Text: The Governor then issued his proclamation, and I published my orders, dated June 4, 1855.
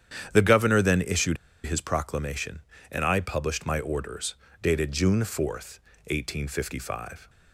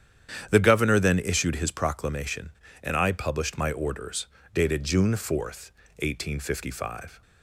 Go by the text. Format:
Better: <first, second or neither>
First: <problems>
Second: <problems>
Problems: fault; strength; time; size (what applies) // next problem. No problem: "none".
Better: second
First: starts louder than the rest; strong; until 1.3 s; 9.5 dB // pauses between "issued" and "his"; slight; at 1.3 s; 0.28 s long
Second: starts louder than the rest; strong; until 1.5 s; 9.5 dB